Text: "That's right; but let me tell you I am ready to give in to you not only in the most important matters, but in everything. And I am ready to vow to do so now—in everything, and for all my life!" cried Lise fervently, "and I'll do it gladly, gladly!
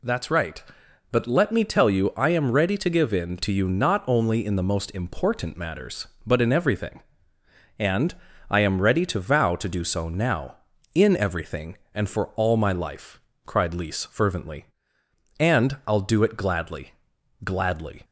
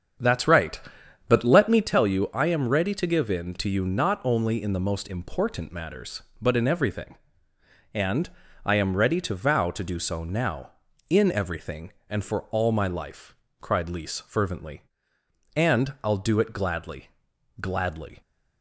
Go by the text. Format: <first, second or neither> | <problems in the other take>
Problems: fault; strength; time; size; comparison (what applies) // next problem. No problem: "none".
first | starts louder than the rest; strong; until 2.0 s; 8 dB // pauses between "And" and "I"; slight; at 8.2 s; 0.34 s long; slight in the first